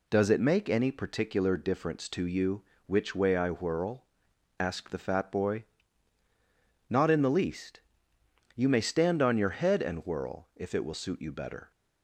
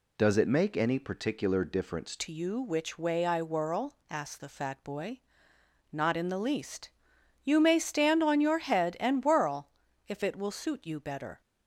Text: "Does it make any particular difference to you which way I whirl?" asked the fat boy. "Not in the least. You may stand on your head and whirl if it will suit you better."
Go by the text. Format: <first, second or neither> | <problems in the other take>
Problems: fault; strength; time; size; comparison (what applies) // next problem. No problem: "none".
first | changes voice at "to"; from 2.1 s on; 9.3 s long // pauses between "whirl" and "if"; at 9.6 s; 0.40 s long